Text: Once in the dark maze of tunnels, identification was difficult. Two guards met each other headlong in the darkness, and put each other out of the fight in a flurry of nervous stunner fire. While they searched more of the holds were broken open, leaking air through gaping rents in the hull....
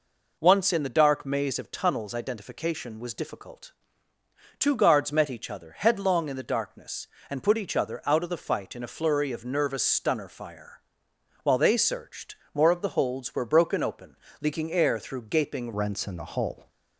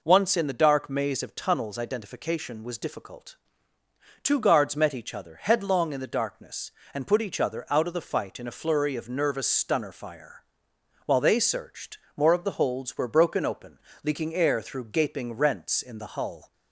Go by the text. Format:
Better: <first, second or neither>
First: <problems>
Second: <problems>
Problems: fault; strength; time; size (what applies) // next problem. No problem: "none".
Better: second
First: pauses between "searched" and "more"; slight; at 12.3 s; 0.18 s long // changes voice at "rents"; from 15.7 s on; 0.9 s long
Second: pauses between "searched" and "more"; slight; at 11.9 s; 0.18 s long